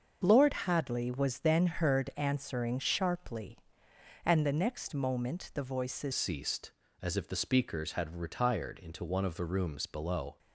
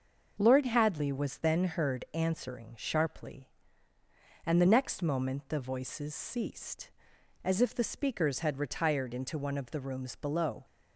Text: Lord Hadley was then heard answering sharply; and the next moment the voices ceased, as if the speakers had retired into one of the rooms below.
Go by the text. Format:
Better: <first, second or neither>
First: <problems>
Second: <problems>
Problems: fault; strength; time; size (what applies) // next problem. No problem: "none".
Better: second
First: starts louder than the rest; until 1.2 s; 6.5 dB // changes voice at "ceased"; from 6.1 s on; 4.2 s long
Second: starts louder than the rest; noticeable; until 1.4 s; 6 dB